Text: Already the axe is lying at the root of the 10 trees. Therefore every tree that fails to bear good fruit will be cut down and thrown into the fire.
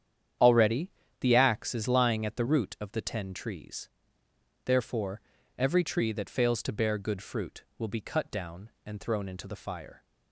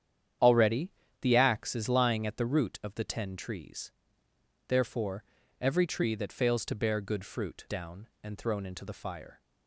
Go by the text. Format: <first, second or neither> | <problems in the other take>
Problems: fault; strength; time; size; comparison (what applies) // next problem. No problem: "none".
first | starts louder than the rest; strong; until 1.7 s; 9 dB; strong in the first // pauses between "Already" and "the"; slight; at 0.9 s; 0.30 s long; slight in the first // pauses between "Therefore" and "every"; slight; at 5.2 s; 0.36 s long; slight in the first // skips "will be cut"; at 7.6 s